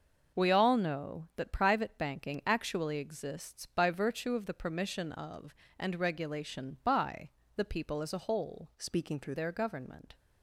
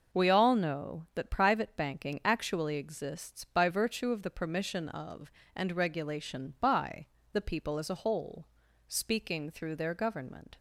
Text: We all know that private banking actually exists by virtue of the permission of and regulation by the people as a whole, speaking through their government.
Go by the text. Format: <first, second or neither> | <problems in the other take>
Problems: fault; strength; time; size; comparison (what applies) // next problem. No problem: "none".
second | starts louder than the rest; noticeable; until 1.4 s; 6 dB // pauses between "by" and "the"; slight; at 7.3 s; 0.26 s long; slight in the second // changes voice from "speaking" to "through"; from 8.7 to 9.3 s; 0.6 s long